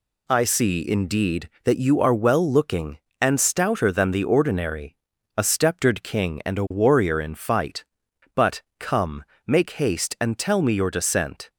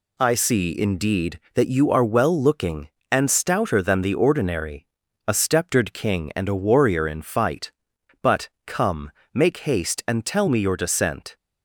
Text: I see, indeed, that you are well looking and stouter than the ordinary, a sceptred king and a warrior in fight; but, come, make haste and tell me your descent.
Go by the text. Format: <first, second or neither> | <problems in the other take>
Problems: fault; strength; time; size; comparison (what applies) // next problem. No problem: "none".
neither | none